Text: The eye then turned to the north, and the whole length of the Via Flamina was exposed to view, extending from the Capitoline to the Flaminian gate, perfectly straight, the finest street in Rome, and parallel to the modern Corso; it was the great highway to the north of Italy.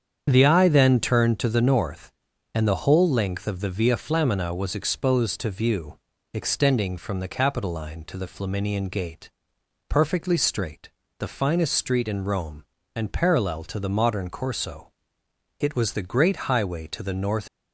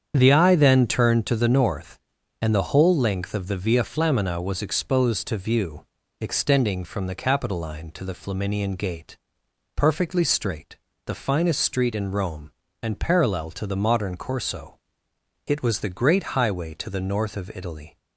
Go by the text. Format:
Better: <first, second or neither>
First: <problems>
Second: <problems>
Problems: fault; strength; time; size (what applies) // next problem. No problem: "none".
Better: second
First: starts louder than the rest; strong; until 1.2 s; 8 dB // stops before "of Italy"; at 17.4 s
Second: starts louder than the rest; strong; until 1.1 s; 8 dB